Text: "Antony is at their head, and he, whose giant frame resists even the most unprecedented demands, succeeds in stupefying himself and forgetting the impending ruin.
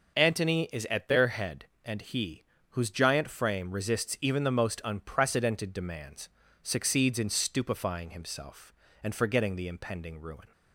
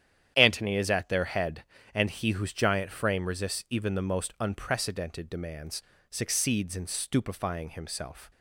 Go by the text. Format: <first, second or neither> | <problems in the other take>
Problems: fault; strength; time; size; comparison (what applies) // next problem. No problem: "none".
first | starts louder than the rest; strong; until 1.3 s; 10 dB; noticeable in the first // stops before "and forgetting the impending ruin"; at 8.3 s